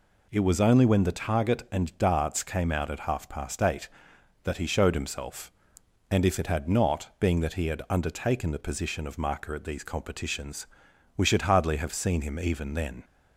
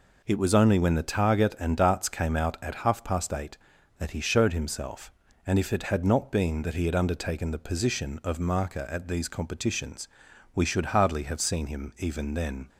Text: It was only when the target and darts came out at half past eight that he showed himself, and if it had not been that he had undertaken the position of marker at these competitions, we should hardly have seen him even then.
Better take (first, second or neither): second